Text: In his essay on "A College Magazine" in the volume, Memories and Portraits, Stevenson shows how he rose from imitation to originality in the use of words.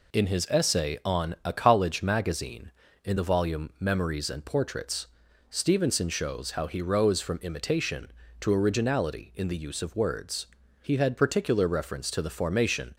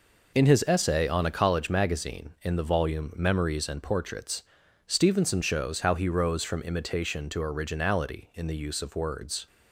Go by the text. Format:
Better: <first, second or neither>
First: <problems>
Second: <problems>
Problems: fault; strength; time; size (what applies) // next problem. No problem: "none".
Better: second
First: goes on to say "He had particular reference to the formation"; strong; from 10.8 s on; 2.1 s long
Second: none